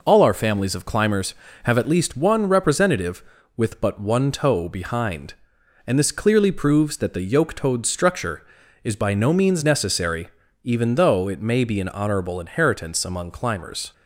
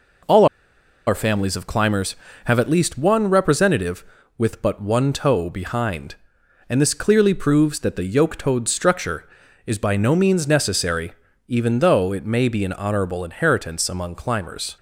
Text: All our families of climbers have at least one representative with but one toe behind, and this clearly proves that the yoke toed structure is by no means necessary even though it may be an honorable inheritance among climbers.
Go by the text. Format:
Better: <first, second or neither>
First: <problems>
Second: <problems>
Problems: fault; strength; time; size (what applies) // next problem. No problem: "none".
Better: first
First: pauses between "necessary" and "even"; slight; at 10.2 s; 0.36 s long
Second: pauses between "All" and "our"; noticeable; at 0.4 s; 0.61 s long // pauses between "necessary" and "even"; slight; at 11.1 s; 0.36 s long